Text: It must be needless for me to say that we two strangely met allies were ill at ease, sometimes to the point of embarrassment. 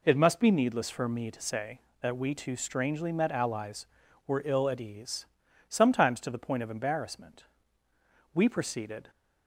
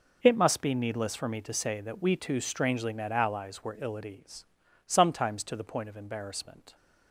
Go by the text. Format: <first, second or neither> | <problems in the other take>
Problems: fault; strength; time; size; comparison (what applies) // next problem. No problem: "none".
second | goes on to say "We proceeded"; noticeable; from 8.3 s on; 0.76 s long